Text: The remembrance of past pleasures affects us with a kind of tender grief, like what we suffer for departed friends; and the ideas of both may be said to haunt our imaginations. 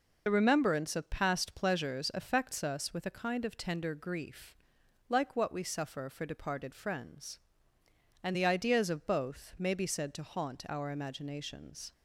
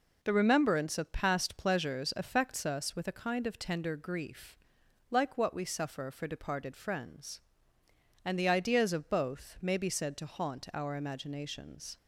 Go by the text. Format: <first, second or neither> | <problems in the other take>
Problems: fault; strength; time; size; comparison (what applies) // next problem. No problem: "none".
second | loses the start of "The"; at 0.2 s; 50 ms